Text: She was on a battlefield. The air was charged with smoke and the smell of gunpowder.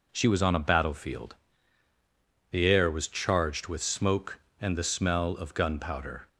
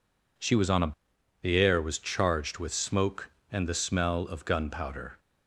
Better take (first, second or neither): first